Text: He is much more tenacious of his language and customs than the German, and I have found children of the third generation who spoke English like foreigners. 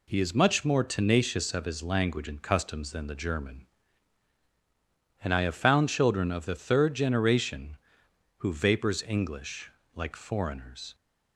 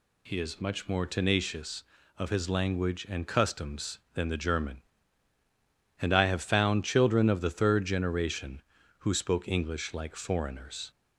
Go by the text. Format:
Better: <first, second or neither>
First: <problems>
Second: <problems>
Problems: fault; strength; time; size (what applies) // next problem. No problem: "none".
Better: second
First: says "vapors" for "spoke"; at 8.5 s // pauses between "English" and "like"; slight; at 9.7 s; 0.24 s long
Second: none